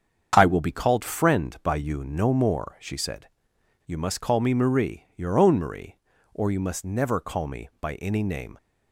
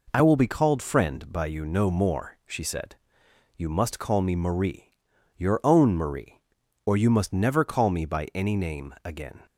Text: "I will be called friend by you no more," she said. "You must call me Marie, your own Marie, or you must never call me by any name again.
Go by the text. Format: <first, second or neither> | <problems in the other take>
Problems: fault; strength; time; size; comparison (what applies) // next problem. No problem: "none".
second | starts louder than the rest; strong; until 1.3 s; 7.5 dB // stops before "again"; at 8.5 s